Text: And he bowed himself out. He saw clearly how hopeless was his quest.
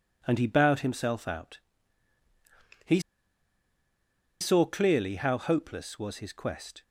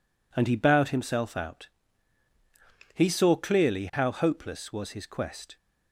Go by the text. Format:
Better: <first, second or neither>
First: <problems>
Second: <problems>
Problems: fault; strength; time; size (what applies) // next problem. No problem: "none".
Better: second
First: pauses between "He" and "saw"; strong; at 2.9 s; 1.4 s long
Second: none